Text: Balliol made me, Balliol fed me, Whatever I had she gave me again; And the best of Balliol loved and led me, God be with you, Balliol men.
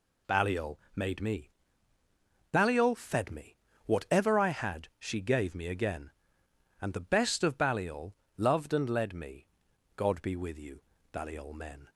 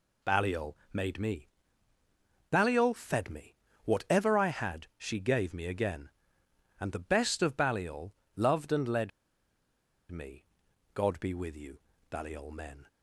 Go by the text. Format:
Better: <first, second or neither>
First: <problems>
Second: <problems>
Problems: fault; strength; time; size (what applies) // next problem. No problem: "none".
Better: first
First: pauses between "Balliol" and "made"; slight; at 0.7 s; 0.16 s long // pauses between "Balliol" and "loved"; slight; at 8.1 s; 0.24 s long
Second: pauses between "Balliol" and "made"; slight; at 0.7 s; 0.16 s long // pauses between "Balliol" and "loved"; slight; at 8.1 s; 0.24 s long // pauses between "led" and "me"; at 9.1 s; 1.0 s long